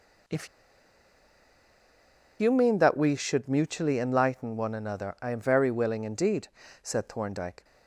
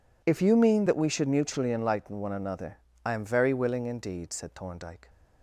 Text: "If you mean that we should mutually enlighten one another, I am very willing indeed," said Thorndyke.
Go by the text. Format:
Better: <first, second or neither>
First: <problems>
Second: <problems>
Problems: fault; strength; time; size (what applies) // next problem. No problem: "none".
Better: second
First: pauses between "If" and "you"; strong; at 0.4 s; 1.9 s long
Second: none